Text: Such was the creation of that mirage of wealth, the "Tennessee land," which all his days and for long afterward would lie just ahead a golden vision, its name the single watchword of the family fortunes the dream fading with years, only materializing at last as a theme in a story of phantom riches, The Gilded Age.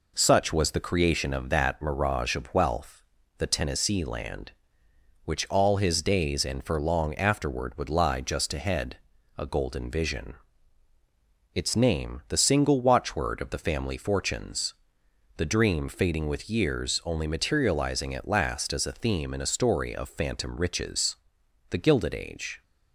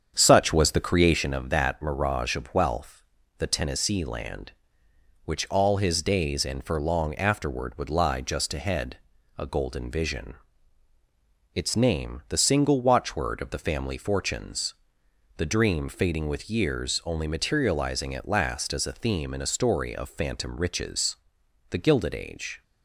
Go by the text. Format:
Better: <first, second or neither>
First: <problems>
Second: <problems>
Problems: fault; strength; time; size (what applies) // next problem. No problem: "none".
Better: first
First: pauses between "ahead" and "a"; at 8.9 s; 0.40 s long // pauses between "fortunes" and "the"; noticeable; at 14.7 s; 0.64 s long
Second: starts louder than the rest; strong; until 1.4 s; 7.5 dB // pauses between "ahead" and "a"; at 8.9 s; 0.40 s long // pauses between "fortunes" and "the"; noticeable; at 14.7 s; 0.64 s long